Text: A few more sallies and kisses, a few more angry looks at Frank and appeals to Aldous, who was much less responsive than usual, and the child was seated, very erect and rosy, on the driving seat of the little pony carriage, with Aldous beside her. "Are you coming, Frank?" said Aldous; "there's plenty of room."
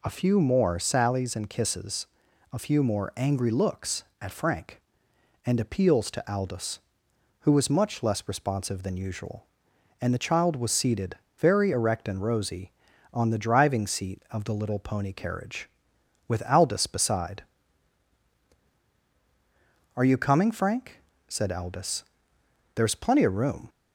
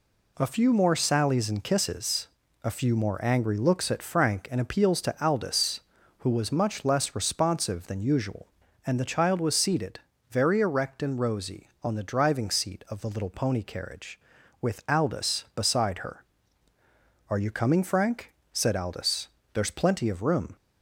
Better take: second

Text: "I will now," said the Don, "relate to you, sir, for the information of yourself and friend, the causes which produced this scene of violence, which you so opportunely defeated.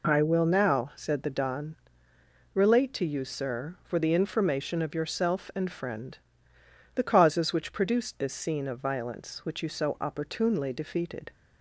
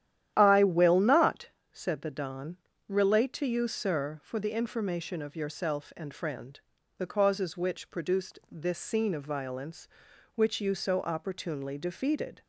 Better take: first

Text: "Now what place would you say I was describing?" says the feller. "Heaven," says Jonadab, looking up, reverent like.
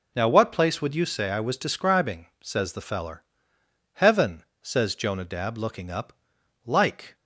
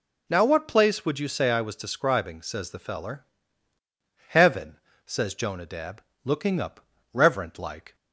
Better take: second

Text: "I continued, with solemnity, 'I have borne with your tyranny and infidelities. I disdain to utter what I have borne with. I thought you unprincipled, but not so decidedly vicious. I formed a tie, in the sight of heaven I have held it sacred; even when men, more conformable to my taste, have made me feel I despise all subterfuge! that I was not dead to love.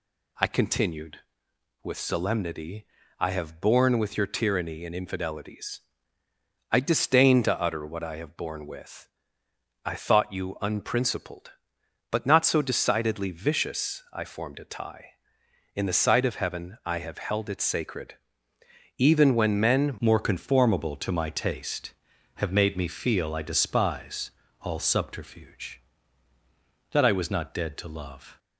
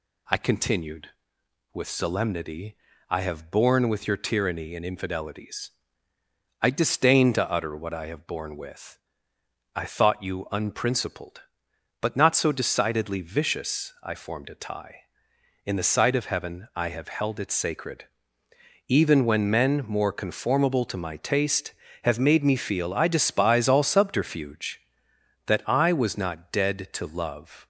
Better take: second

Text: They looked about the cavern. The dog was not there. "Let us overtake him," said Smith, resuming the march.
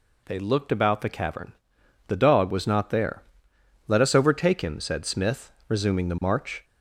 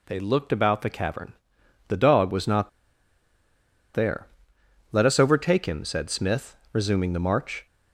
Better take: first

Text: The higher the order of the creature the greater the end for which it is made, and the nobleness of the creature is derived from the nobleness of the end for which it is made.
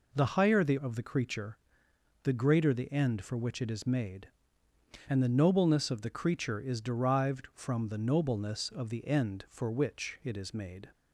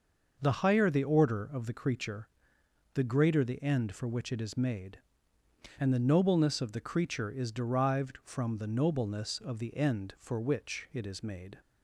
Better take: second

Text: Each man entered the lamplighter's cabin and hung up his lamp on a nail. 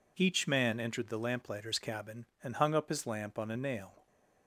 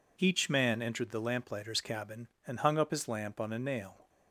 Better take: neither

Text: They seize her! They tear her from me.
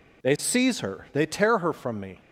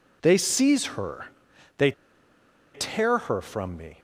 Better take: first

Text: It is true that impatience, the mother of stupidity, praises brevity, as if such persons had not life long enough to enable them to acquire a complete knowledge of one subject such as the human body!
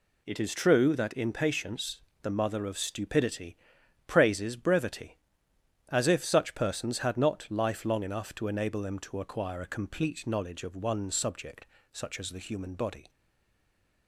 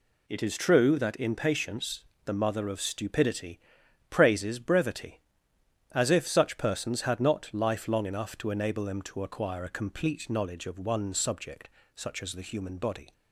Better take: second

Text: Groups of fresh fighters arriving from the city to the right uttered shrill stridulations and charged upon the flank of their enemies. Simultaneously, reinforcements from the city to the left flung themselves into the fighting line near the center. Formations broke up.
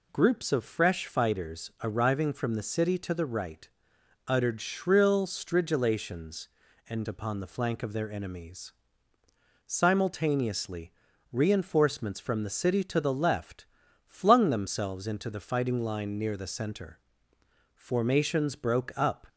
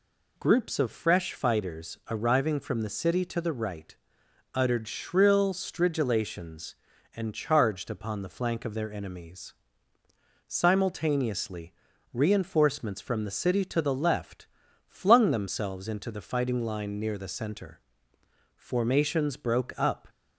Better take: second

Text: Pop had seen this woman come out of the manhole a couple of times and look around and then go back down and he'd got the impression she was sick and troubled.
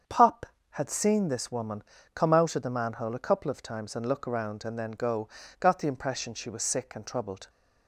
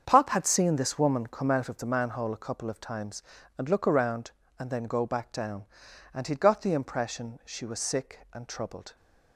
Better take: second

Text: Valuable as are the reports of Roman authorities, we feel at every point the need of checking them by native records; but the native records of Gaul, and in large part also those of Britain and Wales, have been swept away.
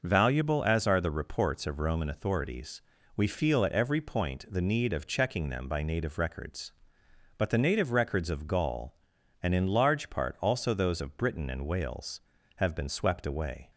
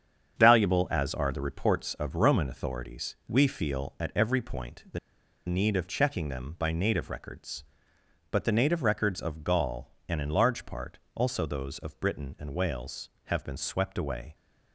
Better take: first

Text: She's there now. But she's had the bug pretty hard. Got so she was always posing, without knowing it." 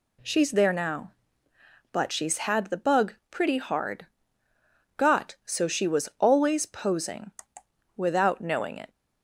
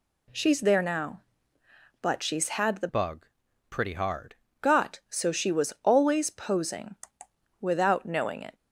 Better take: first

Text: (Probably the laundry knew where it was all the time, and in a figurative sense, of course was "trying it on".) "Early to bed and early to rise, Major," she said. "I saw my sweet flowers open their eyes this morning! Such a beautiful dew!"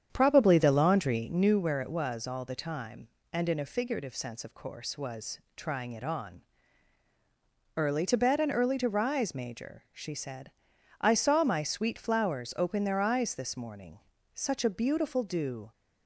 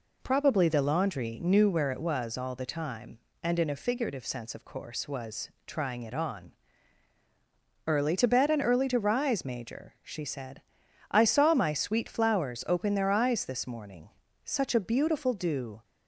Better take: second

